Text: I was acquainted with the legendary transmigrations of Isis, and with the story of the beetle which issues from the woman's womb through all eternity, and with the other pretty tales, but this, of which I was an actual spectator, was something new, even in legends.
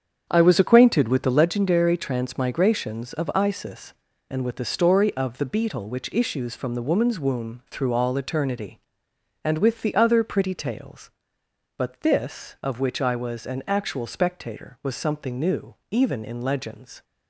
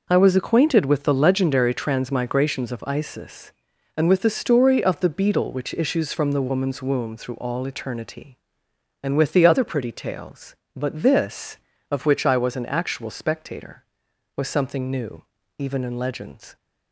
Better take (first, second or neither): second